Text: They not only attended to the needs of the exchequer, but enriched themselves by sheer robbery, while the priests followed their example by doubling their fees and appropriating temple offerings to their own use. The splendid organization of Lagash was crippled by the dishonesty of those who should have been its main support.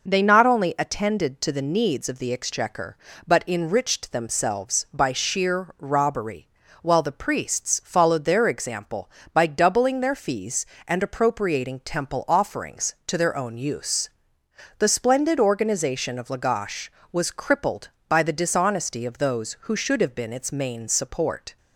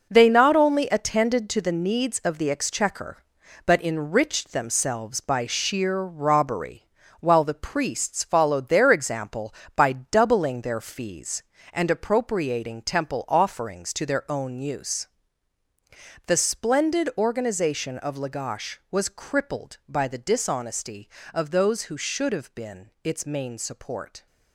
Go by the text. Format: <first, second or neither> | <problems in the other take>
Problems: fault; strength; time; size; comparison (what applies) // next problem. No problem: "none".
first | gets quieter; strong; throughout; 9 dB